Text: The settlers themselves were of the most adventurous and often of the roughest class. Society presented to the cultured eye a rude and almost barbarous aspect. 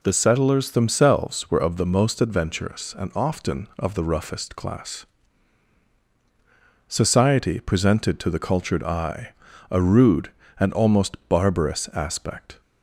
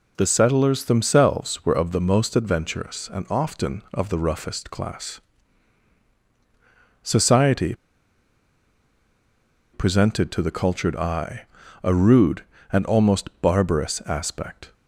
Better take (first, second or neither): first